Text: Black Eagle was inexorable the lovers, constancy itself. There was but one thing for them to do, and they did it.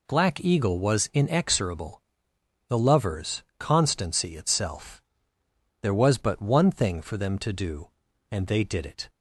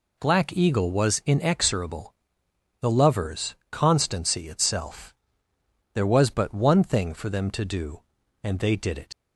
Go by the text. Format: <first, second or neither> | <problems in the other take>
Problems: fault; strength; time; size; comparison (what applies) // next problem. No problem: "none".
first | pauses between "inexorable" and "the"; noticeable; at 2.1 s; 0.66 s long; noticeable in the first // leaves "it" unfinished; at 9.1 s; 90 ms